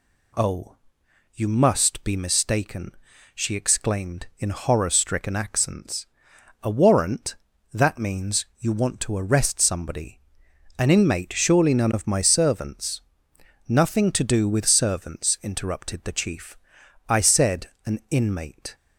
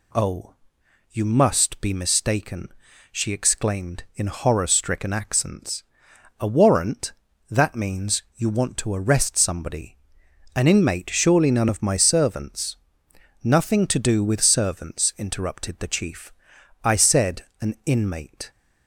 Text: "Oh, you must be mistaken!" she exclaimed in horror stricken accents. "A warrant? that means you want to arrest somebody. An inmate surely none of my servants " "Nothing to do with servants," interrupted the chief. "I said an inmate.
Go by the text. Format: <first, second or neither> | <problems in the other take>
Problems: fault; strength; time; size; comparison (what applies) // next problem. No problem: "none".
neither | pauses between "said" and "an"; slight; the same in both